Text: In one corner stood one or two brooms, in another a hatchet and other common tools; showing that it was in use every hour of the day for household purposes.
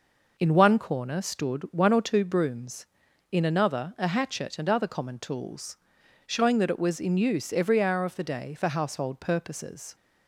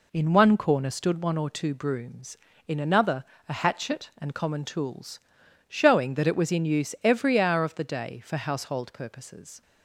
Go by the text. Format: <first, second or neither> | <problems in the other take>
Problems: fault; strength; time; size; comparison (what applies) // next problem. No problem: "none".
first | pauses between "another" and "a"; slight; at 3.2 s; 0.24 s long // skips "other"; at 4.3 s